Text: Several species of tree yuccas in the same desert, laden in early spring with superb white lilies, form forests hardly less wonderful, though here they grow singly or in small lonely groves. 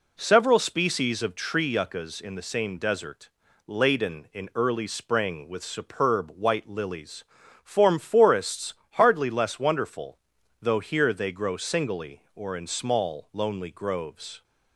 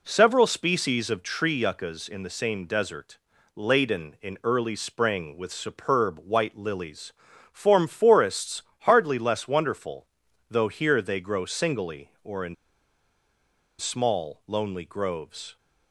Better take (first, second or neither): first